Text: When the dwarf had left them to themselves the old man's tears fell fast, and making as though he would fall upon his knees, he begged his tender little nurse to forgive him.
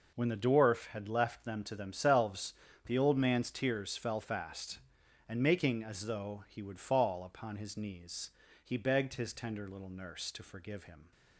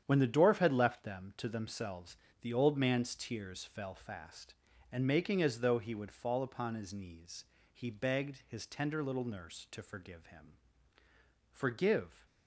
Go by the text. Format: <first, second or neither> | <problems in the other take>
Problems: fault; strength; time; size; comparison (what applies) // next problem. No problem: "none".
first | starts louder than the rest; strong; until 1.0 s; 9 dB // pauses between "themselves" and "the"; slight; at 2.1 s; 0.24 s long; slight in the first // goes on to say "Forgive"; noticeable; from 11.5 s on; 0.74 s long